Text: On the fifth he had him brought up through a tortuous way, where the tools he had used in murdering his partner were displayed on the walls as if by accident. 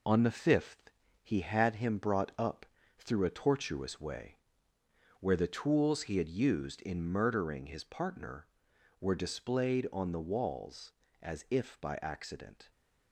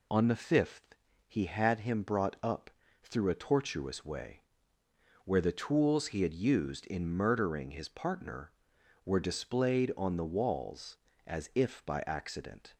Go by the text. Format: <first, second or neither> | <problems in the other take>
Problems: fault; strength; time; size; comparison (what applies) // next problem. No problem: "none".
second | gets quieter; noticeable; throughout; 4.5 dB // pauses between "fifth" and "he"; slight; at 0.9 s; 0.32 s long; slight in the second // pauses between "up" and "through"; slight; at 2.6 s; 0.34 s long; slight in the second